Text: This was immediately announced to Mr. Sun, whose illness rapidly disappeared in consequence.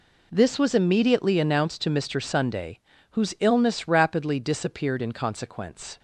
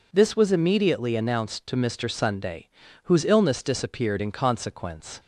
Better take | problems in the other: first | skips "rapidly"; at 3.6 s

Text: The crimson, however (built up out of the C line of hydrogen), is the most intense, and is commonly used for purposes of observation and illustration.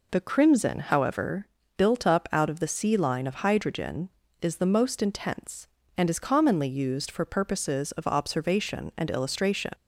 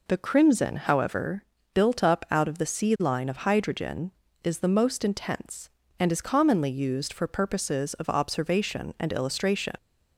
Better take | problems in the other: neither | none

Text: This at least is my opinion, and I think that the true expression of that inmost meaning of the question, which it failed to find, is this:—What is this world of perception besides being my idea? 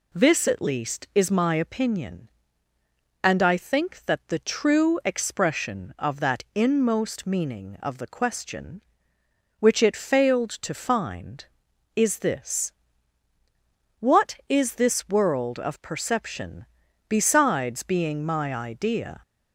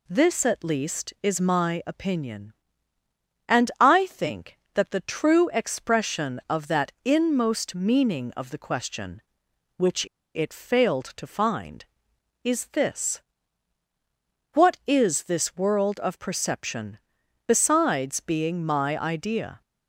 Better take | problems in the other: first | pauses between "which" and "it"; slight; at 10.0 s; 0.29 s long // pauses between "perception" and "besides"; noticeable; at 16.9 s; 0.48 s long; also in the first

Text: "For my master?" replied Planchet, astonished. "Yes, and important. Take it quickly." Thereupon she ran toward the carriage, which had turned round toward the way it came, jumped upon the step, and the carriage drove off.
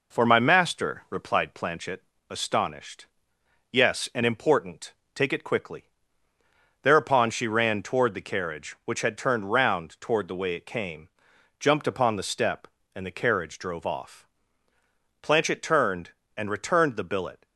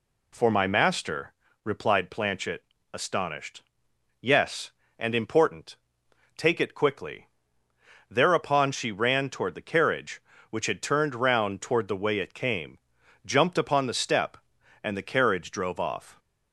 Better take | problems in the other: second | goes on to say "Planchet turned and returned the billet"; strong; from 15.2 s on; 2.2 s long

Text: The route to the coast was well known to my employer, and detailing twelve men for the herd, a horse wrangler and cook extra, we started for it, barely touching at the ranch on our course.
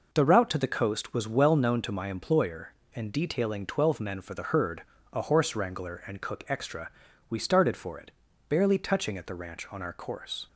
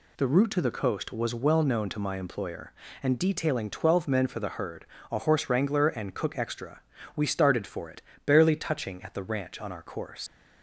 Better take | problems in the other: first | leaves "course" unfinished; at 10.2 s; 105 ms

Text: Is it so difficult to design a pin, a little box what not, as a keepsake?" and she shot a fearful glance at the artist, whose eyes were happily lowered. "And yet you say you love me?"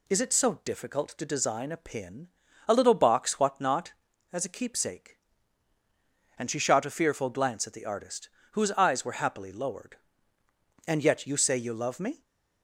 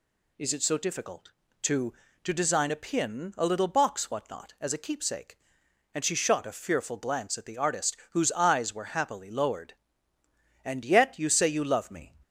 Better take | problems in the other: first | says "to" twice; at 2.2 s

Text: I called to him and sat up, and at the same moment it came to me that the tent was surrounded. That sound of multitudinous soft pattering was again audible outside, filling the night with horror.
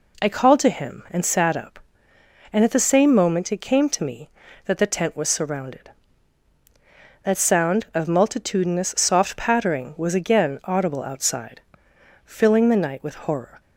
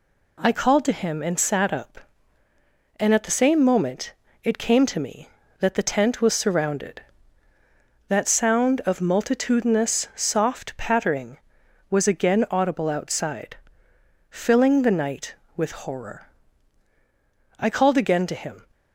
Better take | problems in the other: first | pauses between "moment" and "it"; slight; at 4.1 s; 0.32 s long // goes on to say "I called again to him"; noticeable; from 17.5 s on; 1.0 s long

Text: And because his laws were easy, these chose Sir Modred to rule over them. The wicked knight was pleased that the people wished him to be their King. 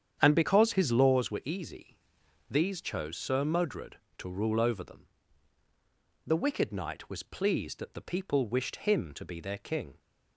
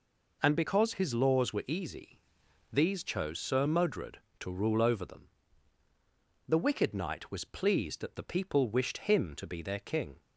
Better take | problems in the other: second | starts louder than the rest; strong; until 1.2 s; 8.5 dB

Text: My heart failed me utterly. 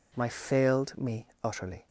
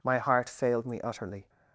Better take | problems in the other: second | skips "heart"; at 0.2 s // pauses between "me" and "utterly"; slight; at 1.2 s; 0.18 s long

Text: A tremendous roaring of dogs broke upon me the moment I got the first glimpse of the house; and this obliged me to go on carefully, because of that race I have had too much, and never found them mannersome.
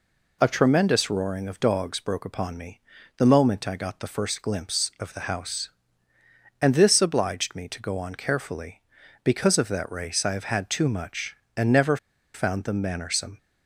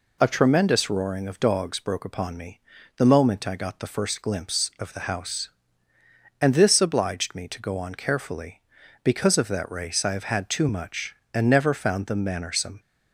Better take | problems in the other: second | pauses between "me" and "the"; at 2.7 s; 0.38 s long; also in the second // pauses between "never" and "found"; at 11.9 s; 0.37 s long

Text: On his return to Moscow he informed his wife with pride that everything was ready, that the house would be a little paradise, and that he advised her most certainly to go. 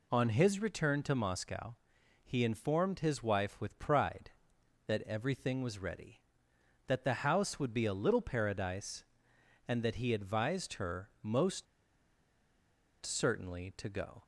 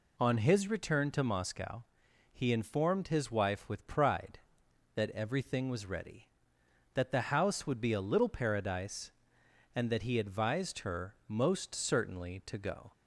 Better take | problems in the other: second | pauses between "Moscow" and "he"; noticeable; at 1.7 s; 0.50 s long; noticeable in the second // pauses between "most" and "certainly"; strong; at 11.6 s; 1.3 s long

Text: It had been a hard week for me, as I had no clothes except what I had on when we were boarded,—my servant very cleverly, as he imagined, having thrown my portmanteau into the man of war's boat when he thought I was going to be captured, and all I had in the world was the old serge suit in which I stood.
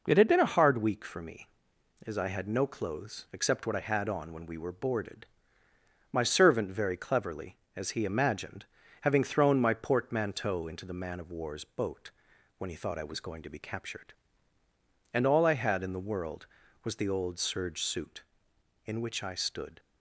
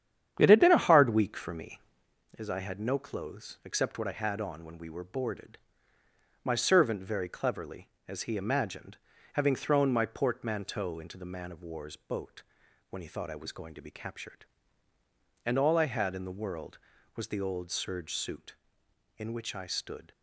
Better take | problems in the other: first | starts louder than the rest; strong; until 2.1 s; 9 dB // pauses between "boat" and "when"; noticeable; at 12.4 s; 0.46 s long; noticeable in the first

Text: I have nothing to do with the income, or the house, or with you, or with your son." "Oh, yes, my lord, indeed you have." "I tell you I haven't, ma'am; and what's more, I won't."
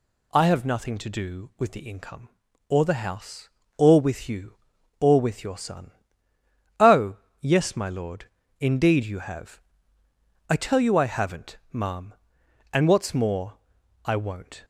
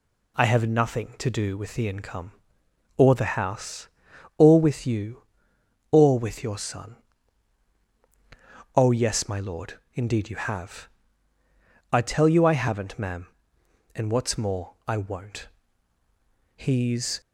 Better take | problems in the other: first | goes on to say "He's"; noticeable; from 16.5 s on; 0.64 s long

